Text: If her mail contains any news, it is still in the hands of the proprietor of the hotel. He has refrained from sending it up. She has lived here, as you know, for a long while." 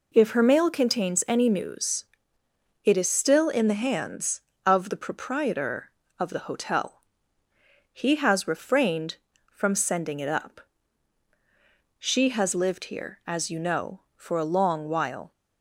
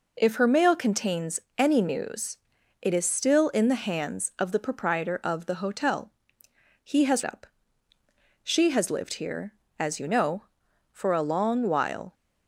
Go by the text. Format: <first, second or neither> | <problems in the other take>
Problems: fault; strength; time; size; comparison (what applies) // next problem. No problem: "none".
first | pauses between "contains" and "any"; slight; at 1.3 s; 0.18 s long // skips "refrained from sending it"; at 7.2 s